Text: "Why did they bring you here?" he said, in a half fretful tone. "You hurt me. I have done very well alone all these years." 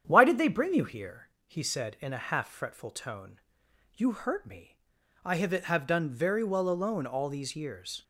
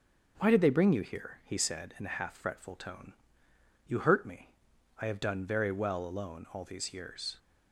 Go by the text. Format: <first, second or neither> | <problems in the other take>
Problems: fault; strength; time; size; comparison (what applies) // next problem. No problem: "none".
second | starts louder than the rest; strong; until 1.0 s; 8.5 dB; also in the second // says "have" twice; at 5.5 s